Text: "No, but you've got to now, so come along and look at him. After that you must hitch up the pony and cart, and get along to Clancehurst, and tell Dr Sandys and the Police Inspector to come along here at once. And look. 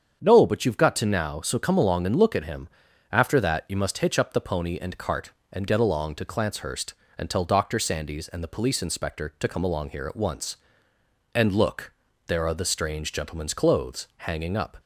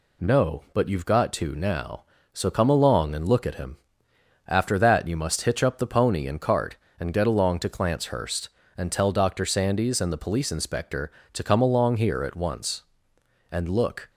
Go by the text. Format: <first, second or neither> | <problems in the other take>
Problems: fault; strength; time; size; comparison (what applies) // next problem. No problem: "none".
second | starts louder than the rest; strong; until 1.2 s; 7.5 dB // goes on to say "There are the strange gentleman's clothes hanging up"; strong; from 12.2 s on; 2.5 s long